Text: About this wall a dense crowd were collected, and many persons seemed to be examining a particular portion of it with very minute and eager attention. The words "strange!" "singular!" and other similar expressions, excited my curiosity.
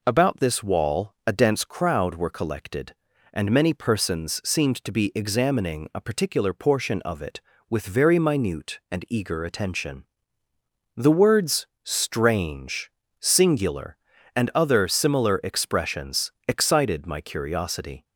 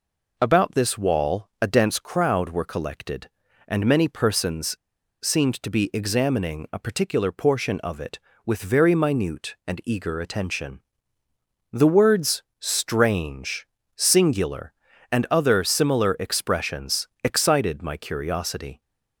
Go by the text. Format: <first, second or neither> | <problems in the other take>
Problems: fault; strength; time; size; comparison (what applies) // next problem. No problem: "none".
first | pauses between "persons" and "seemed"; noticeable; at 4.7 s; 0.47 s long // pauses between "words" and "strange"; slight; at 12.4 s; 0.18 s long; slight in the first